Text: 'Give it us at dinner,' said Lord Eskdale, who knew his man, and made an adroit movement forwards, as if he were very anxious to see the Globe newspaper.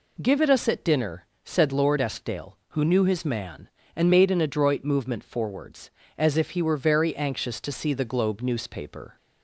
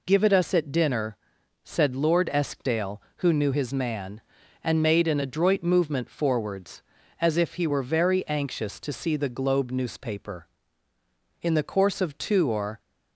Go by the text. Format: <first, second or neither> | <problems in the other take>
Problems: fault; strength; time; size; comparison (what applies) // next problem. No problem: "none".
first | goes on to say "In the course of two or"; from 11.4 s on; 1.3 s long